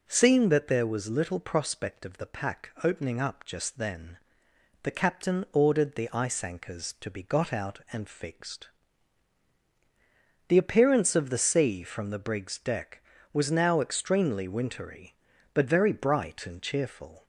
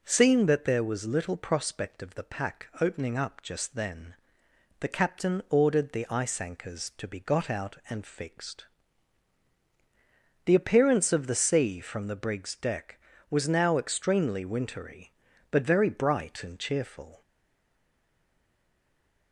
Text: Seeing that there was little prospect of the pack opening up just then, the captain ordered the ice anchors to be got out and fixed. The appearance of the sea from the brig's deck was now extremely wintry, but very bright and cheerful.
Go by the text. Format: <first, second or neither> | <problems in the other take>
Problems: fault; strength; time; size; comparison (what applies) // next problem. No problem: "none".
first | stays silent after the last word; from 17.2 s on; 2.1 s long